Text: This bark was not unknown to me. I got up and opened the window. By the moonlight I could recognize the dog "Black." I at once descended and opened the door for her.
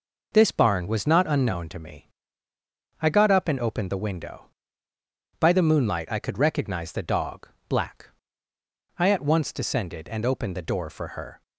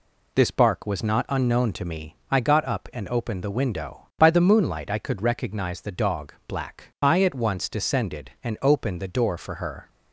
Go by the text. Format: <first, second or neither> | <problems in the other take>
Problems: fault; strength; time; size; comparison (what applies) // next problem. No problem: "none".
second | says "barn" for "bark"; at 0.5 s // pauses between "dog" and "Black"; slight; at 7.5 s; 0.18 s long